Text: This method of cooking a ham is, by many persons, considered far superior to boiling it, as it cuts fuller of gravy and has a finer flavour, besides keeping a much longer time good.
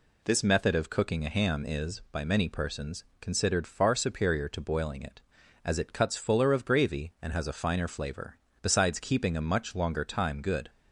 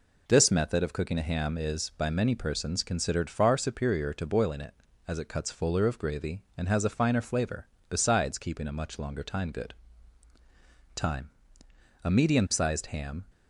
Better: first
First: none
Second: goes on to say "Time A medium sized ham"; strong; from 10.9 s on; 2.2 s long

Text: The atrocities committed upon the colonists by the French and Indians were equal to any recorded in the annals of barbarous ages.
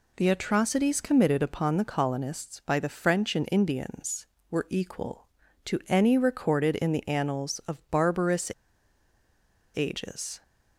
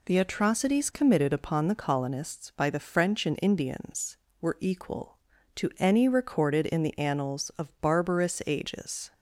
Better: second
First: pauses between "barbarous" and "ages"; at 8.5 s; 1.2 s long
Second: none

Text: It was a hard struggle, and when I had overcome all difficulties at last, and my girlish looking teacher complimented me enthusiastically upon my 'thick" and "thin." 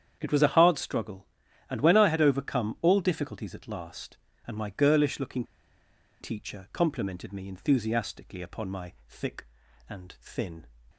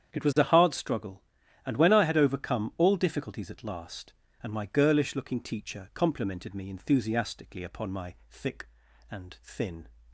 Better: second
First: starts louder than the rest; strong; until 1.2 s; 8.5 dB // pauses between "looking" and "teacher"; noticeable; at 5.4 s; 0.76 s long // pauses between "my" and "thick"; slight; at 8.9 s; 0.16 s long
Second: starts louder than the rest; strong; until 1.1 s; 8.5 dB // pauses between "my" and "thick"; slight; at 8.1 s; 0.16 s long

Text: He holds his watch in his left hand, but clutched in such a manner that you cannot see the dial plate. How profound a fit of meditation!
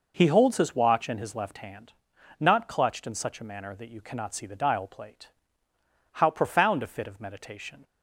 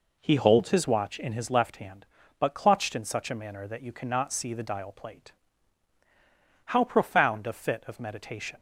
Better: second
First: says "not" for "but"; at 2.3 s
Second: none

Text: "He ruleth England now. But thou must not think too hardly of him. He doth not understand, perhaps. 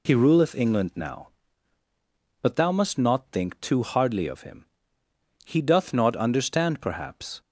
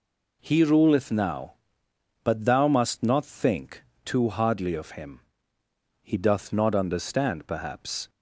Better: first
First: none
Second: skips "England"; at 1.1 s // pauses between "think" and "too"; slight; at 3.8 s; 0.22 s long

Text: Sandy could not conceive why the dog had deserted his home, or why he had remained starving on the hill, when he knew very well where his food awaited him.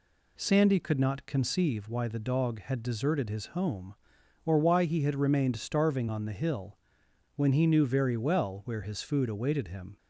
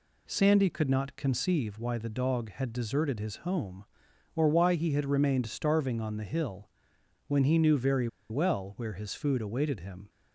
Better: first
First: none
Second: pauses between "very" and "well"; slight; at 8.0 s; 0.22 s long

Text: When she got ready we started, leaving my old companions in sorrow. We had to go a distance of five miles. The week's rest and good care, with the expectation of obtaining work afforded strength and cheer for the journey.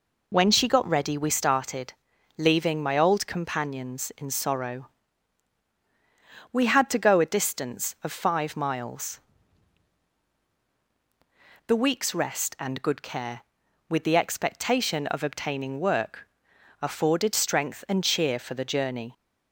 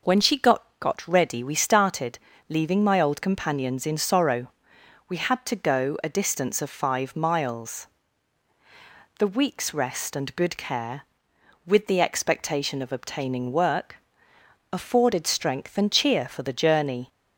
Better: first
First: pauses between "work" and "afforded"; noticeable; at 16.2 s; 0.54 s long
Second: says "got" twice; at 0.8 s // pauses between "work" and "afforded"; noticeable; at 13.9 s; 0.78 s long

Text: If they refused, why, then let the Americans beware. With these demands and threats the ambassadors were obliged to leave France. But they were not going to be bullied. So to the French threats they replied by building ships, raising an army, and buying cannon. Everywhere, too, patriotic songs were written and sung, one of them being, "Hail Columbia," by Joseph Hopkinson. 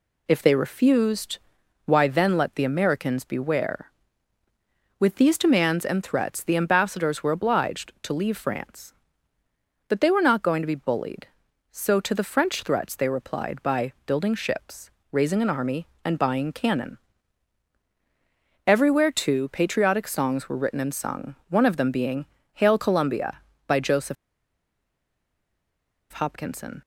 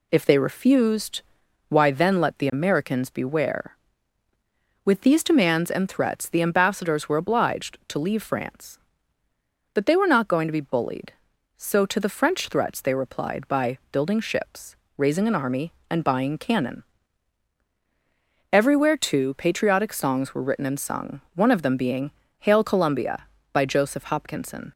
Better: second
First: pauses between "Joseph" and "Hopkinson"; strong; at 24.1 s; 1.9 s long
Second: none

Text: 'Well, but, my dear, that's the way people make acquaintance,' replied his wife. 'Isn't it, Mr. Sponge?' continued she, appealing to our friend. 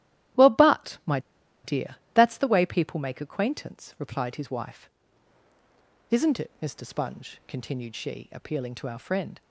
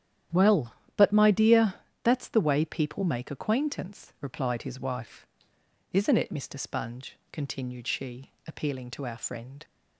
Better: second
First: starts louder than the rest; strong; until 1.9 s; 13 dB // pauses between "my" and "dear"; at 1.1 s; 0.45 s long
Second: starts louder than the rest; strong; until 1.5 s; 10.5 dB

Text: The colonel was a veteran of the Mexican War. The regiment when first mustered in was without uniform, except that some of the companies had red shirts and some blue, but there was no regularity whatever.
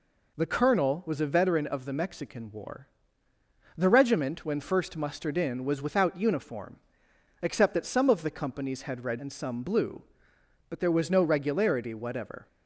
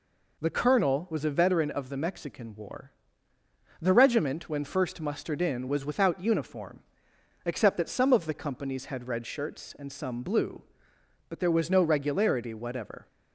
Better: second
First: skips "shirts"; at 9.1 s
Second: none

